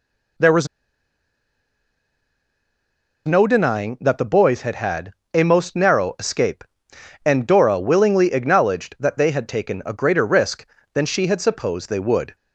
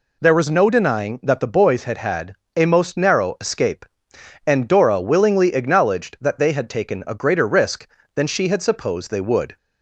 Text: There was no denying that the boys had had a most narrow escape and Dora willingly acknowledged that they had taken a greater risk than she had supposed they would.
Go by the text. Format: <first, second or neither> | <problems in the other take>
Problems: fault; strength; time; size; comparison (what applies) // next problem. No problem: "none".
second | pauses between "was" and "no"; strong; at 0.6 s; 2.5 s long // pauses between "had" and "a"; slight; at 5.1 s; 0.22 s long; slight in the second